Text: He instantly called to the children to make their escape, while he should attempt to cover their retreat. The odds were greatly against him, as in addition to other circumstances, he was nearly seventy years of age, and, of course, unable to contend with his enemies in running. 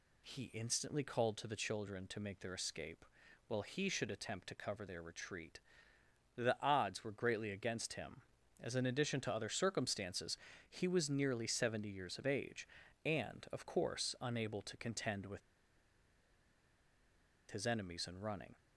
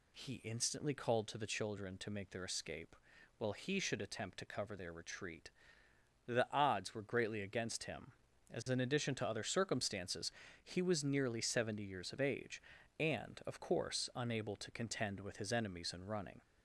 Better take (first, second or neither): second